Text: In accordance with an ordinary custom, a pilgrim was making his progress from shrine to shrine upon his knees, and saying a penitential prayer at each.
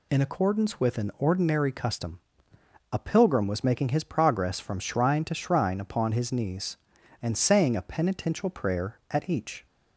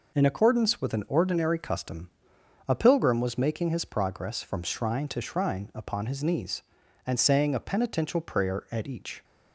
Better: neither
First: none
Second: none

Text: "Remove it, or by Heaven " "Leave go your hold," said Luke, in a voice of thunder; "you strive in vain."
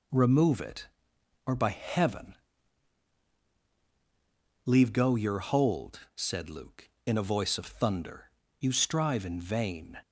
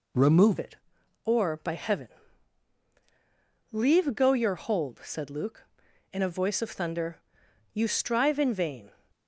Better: first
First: none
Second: changes voice at "it"; from 0.5 s on; 8.4 s long

